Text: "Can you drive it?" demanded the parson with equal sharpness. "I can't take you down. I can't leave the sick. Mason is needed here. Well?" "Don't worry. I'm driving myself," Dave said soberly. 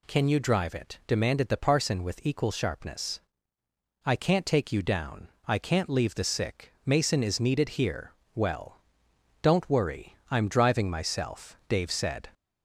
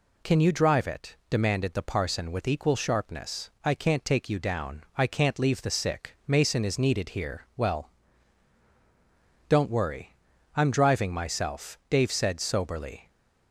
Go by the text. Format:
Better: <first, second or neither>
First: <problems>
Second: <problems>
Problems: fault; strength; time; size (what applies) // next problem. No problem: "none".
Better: second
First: stops before "soberly"; at 12.3 s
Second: none